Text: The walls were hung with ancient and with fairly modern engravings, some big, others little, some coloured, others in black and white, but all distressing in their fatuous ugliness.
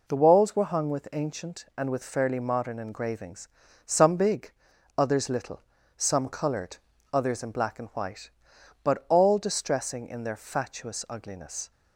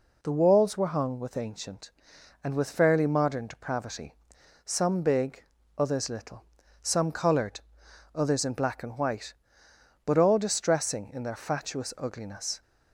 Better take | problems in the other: first | says "depravity" for "engravings"; at 3.4 s

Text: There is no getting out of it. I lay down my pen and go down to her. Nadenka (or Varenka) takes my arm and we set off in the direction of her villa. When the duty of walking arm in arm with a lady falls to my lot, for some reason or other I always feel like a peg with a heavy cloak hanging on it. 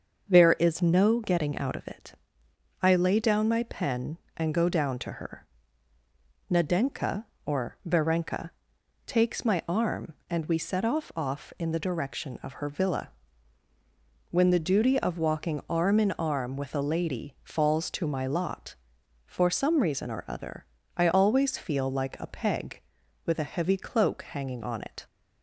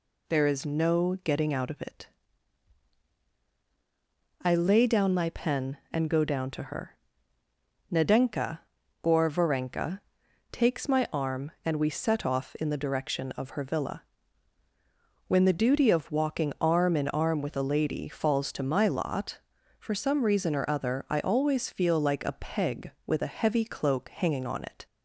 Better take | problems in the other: second | starts louder than the rest; until 1.3 s; 6.5 dB // says "off" twice; at 11.1 s // pauses between "other" and "I"; slight; at 20.6 s; 0.32 s long

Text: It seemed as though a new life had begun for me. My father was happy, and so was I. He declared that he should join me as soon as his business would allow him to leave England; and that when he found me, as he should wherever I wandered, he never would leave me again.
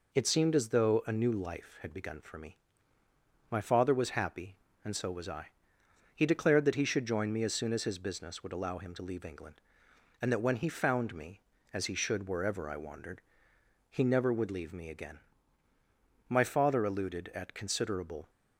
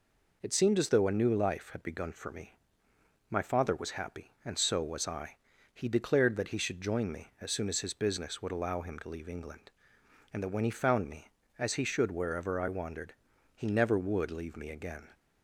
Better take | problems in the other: second | goes on to say "My father alluded at considerable"; strong; from 16.2 s on; 2.0 s long

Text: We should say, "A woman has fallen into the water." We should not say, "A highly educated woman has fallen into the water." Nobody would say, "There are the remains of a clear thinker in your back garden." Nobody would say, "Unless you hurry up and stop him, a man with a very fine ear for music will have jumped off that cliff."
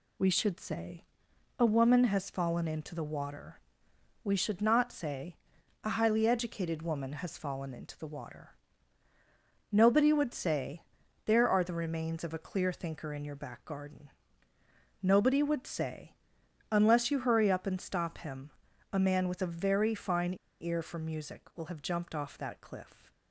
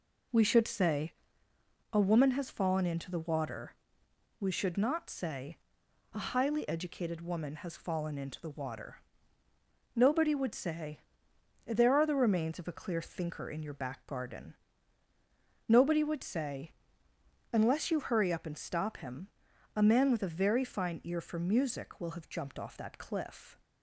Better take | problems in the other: second | pauses between "fine" and "ear"; slight; at 20.3 s; 0.27 s long

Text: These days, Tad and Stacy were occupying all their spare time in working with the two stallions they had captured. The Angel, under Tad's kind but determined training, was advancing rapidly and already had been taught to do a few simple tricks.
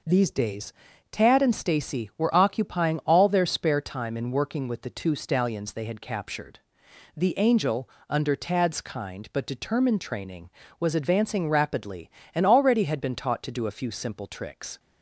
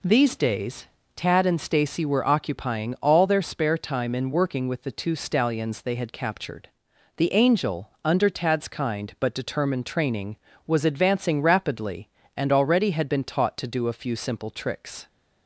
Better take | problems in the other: neither | none

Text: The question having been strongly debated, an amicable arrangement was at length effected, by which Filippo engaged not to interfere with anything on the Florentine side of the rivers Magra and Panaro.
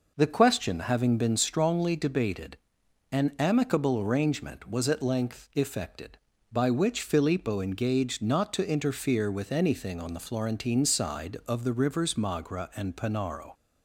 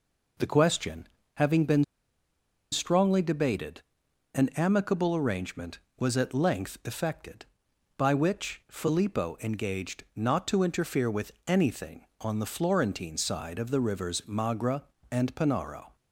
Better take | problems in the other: first | pauses between "question" and "having"; slight; at 1.0 s; 0.26 s long // pauses between "been" and "strongly"; noticeable; at 1.8 s; 0.87 s long // pauses between "with" and "anything"; slight; at 11.3 s; 0.16 s long

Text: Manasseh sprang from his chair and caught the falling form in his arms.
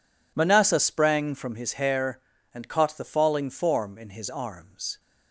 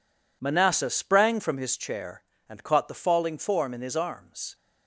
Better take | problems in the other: second | says "hair" for "chair"; at 1.7 s

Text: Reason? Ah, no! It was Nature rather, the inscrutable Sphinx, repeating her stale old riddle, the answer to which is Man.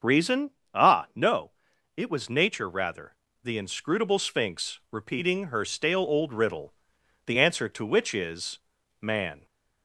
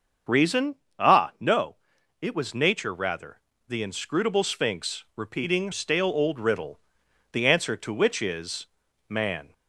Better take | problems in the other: first | starts louder than the rest; until 1.6 s; 6.5 dB; also in the first // skips "her"; at 5.7 s // pauses between "is" and "Man"; at 8.6 s; 0.42 s long; also in the first

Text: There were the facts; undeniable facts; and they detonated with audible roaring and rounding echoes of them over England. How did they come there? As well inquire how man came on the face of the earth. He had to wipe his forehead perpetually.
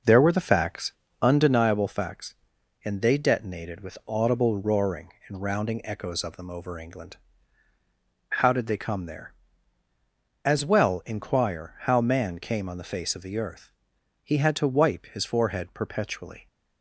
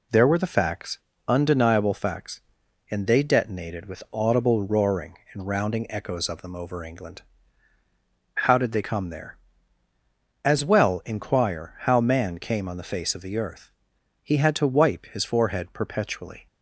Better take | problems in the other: second | starts louder than the rest; noticeable; until 1.6 s; 5.5 dB

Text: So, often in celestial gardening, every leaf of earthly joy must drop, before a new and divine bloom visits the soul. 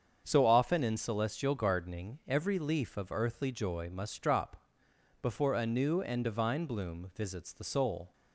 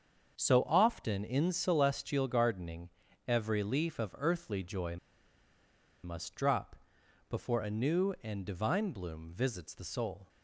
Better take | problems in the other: first | starts louder than the rest; until 1.3 s; 7 dB; also in the first // pauses between "joy" and "must"; at 4.9 s; 1.0 s long

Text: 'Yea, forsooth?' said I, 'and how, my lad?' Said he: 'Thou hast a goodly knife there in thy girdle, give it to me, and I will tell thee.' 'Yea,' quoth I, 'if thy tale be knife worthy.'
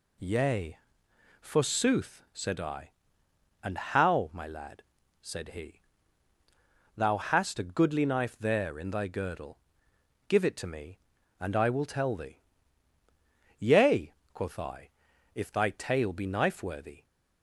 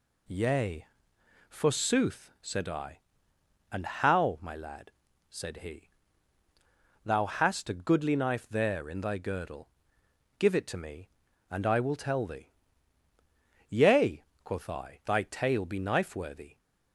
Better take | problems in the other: first | skips "if"; at 15.0 s

